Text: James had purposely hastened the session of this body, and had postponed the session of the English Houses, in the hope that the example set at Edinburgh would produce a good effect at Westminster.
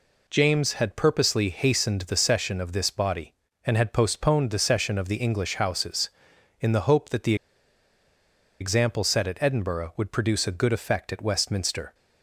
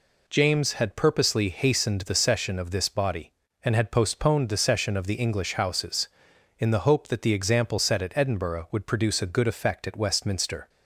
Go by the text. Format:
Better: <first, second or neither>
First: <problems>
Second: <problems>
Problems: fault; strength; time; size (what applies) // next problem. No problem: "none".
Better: second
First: pauses between "the" and "example"; strong; at 7.3 s; 1.2 s long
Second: none